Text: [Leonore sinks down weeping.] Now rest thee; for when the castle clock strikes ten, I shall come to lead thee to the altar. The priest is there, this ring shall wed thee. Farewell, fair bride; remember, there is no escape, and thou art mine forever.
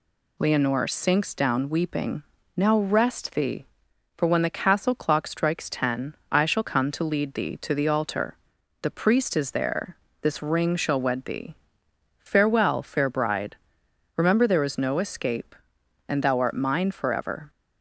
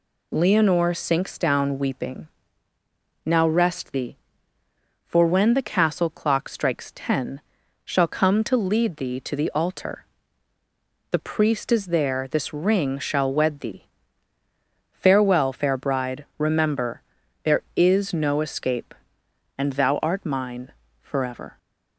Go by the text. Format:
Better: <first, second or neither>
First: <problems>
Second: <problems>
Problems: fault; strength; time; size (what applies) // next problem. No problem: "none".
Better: first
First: none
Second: skips "I"; at 7.6 s // pauses between "mine" and "forever"; slight; at 20.7 s; 0.32 s long